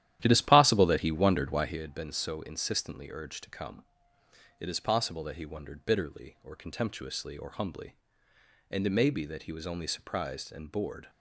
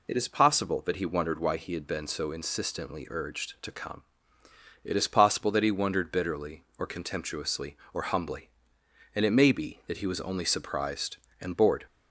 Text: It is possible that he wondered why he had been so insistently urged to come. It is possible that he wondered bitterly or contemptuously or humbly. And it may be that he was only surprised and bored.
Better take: second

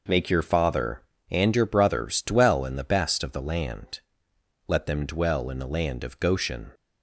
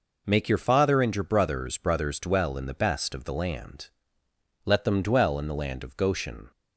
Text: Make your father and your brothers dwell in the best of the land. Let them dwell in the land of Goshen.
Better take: first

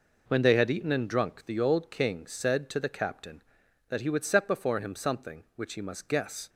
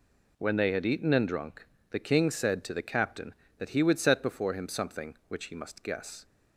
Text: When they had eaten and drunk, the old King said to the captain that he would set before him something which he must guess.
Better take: first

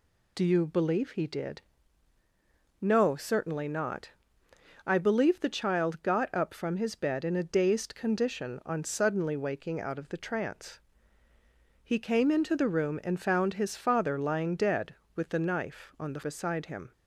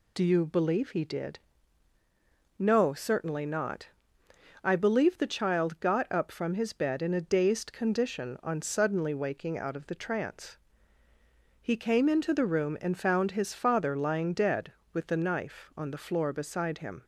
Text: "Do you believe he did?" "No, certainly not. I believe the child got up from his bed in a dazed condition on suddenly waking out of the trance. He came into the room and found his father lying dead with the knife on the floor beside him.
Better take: second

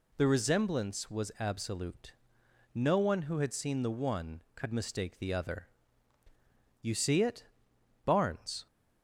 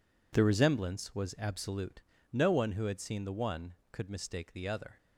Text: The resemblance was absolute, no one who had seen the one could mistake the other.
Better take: second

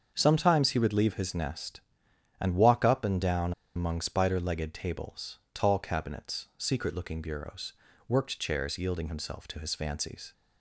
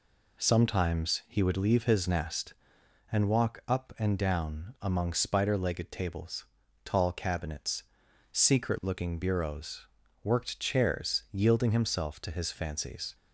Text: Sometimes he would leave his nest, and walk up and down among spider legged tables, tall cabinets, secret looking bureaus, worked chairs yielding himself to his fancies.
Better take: second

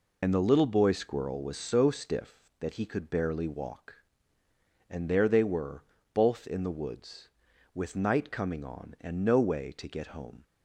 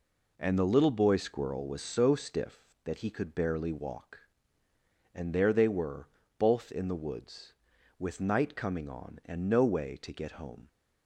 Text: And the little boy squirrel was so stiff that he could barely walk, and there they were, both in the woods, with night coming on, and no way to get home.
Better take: second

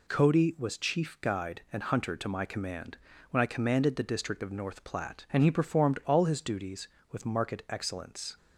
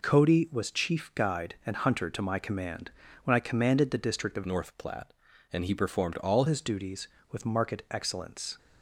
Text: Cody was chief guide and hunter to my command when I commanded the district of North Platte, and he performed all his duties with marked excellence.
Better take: first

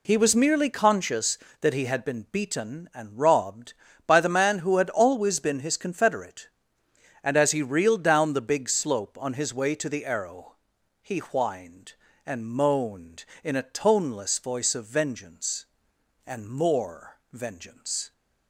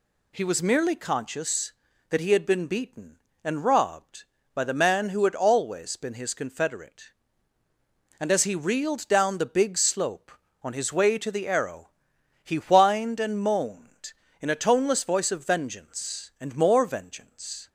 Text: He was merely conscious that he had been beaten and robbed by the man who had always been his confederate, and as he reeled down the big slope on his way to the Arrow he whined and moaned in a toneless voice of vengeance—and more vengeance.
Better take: neither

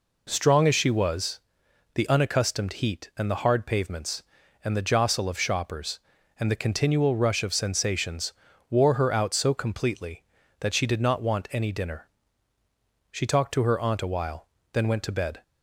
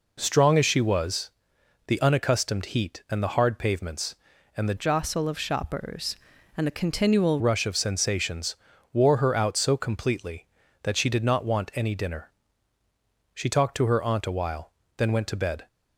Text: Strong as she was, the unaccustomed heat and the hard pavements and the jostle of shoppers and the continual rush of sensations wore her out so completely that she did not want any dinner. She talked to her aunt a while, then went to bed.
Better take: first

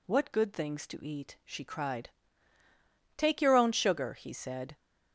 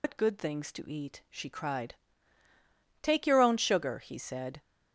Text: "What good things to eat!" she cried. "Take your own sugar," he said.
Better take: first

